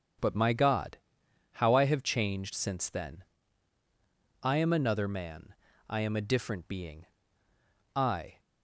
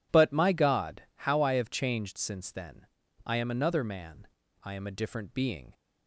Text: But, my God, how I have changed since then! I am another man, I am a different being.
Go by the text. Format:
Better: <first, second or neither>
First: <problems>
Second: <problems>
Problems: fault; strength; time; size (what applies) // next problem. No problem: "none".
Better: second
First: starts louder than the rest; strong; until 1.7 s; 7.5 dB // goes on to say "I"; slight; from 7.9 s on; 0.44 s long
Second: none